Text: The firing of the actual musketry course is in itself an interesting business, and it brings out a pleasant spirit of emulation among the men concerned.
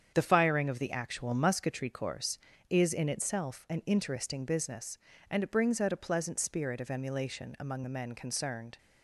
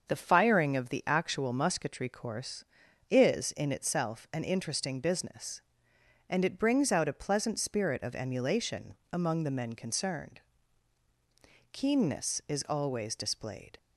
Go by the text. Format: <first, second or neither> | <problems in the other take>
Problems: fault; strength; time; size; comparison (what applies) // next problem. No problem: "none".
first | starts louder than the rest; until 1.1 s; 6.5 dB; strong in the first // pauses between "emulation" and "among"; slight; at 8.9 s; 0.16 s long // goes on to say "Keenness is always displayed"; strong; from 11.7 s on; 2.0 s long